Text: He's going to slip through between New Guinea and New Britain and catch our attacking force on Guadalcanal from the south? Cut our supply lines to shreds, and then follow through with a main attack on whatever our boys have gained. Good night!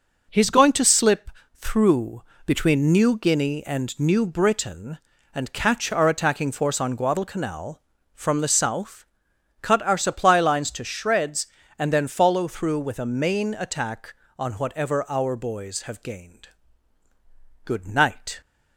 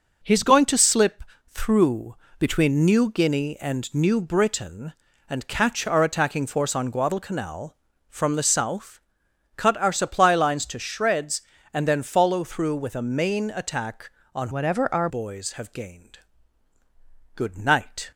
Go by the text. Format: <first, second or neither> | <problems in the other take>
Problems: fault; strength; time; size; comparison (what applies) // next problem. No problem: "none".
first | pauses between "slip" and "through"; slight; at 1.2 s; 0.26 s long; slight in the first // pauses between "through" and "between"; slight; at 2.1 s; 0.24 s long; slight in the first // changes voice from "whatever" to "our"; from 14.5 to 15.0 s; 0.5 s long